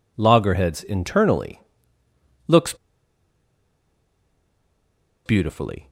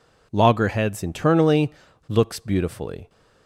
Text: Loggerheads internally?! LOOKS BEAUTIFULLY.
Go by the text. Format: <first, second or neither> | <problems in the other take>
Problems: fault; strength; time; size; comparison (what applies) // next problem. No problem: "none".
second | pauses between "LOOKS" and "BEAUTIFULLY"; strong; at 2.7 s; 2.5 s long